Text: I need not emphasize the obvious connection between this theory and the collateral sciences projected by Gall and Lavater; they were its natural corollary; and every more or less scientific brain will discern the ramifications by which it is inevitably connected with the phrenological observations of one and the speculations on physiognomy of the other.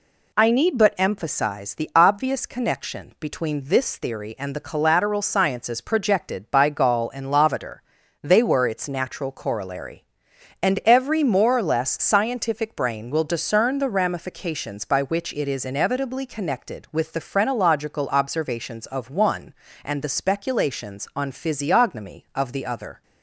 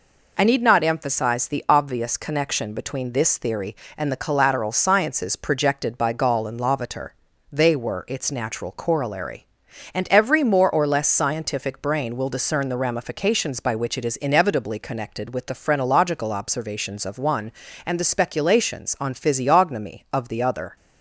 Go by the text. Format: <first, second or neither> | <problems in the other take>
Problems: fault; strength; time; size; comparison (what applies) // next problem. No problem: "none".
second | says "but" for "not"; at 0.7 s